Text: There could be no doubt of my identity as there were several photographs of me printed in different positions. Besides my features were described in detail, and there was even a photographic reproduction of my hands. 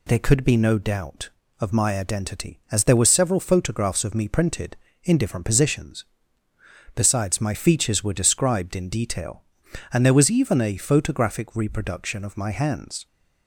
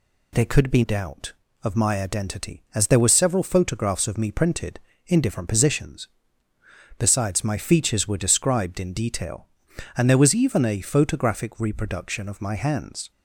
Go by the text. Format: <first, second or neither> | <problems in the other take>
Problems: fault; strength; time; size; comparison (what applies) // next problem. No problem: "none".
first | skips "no"; at 0.8 s